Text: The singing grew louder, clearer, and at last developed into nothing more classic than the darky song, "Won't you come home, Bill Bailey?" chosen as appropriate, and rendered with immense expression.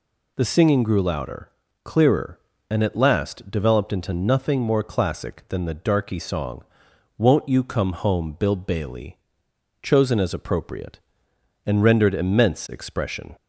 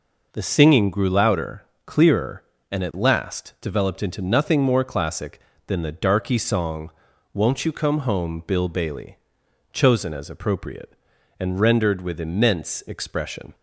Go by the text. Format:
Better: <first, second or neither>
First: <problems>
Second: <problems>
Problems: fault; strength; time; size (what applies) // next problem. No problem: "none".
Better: second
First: skips "with"; at 12.1 s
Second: none